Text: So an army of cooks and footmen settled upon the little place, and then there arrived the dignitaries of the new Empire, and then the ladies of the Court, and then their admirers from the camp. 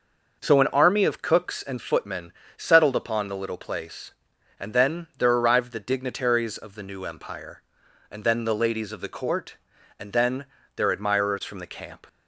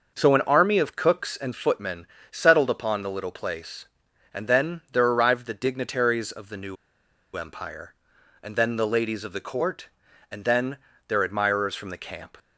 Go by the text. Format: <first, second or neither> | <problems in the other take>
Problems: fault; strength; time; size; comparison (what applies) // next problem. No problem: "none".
first | pauses between "footmen" and "settled"; slight; at 2.0 s; 0.24 s long; slight in the first // pauses between "new" and "Empire"; noticeable; at 6.7 s; 0.60 s long // pauses between "then" and "their"; slight; at 10.7 s; 0.30 s long; slight in the first